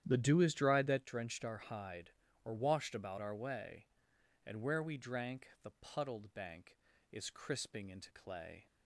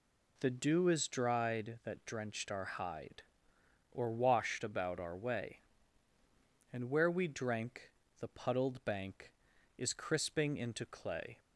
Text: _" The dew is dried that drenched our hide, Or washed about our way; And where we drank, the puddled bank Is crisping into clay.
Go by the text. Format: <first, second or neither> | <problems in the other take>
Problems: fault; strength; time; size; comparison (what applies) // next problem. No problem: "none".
second | starts louder than the rest; strong; until 1.1 s; 10.5 dB